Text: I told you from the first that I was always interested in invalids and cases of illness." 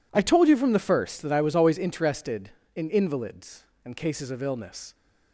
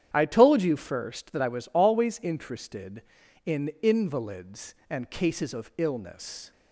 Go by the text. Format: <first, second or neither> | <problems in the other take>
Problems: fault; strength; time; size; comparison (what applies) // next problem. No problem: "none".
first | starts louder than the rest; strong; until 1.1 s; 10 dB // skips "from the"; at 0.7 s